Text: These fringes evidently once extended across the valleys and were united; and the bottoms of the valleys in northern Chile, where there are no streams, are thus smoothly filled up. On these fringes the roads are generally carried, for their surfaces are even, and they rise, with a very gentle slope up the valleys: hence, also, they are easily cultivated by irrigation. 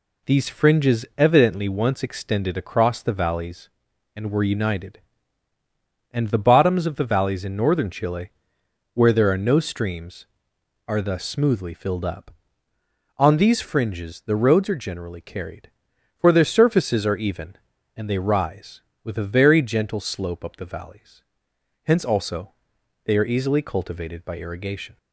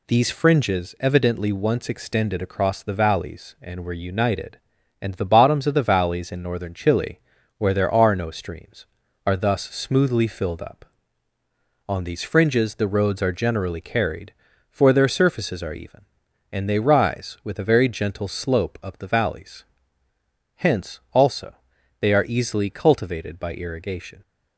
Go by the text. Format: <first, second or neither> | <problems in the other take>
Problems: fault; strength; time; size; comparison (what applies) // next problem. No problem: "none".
neither | none